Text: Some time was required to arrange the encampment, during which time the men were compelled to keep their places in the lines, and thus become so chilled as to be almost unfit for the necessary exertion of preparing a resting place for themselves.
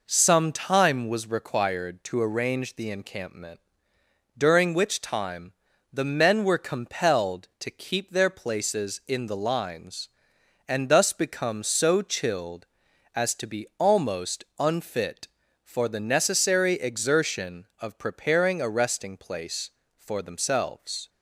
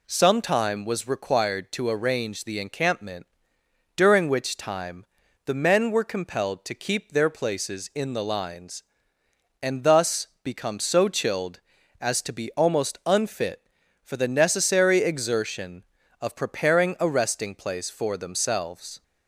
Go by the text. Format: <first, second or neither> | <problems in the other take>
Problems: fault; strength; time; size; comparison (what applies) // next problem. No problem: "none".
neither | pauses between "time" and "the"; the same in both